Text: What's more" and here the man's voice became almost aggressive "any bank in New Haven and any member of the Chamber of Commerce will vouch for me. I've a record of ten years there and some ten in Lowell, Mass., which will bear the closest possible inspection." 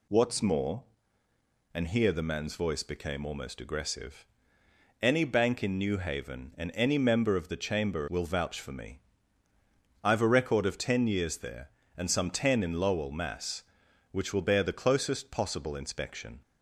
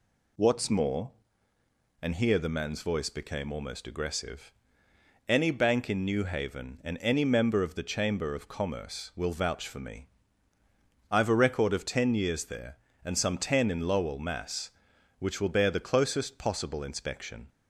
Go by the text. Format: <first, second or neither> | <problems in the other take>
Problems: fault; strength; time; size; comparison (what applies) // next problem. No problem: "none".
second | pauses between "aggressive" and "any"; noticeable; at 4.2 s; 0.78 s long; noticeable in the second // skips "of Commerce"; at 8.0 s